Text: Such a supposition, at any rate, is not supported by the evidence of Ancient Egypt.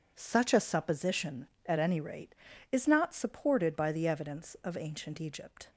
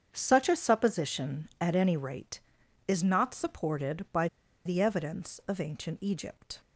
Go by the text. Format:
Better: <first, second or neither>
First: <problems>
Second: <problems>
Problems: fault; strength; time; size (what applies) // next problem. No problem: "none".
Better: first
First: none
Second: starts louder than the rest; strong; until 1.1 s; 7.5 dB // pauses between "by" and "the"; at 4.2 s; 0.38 s long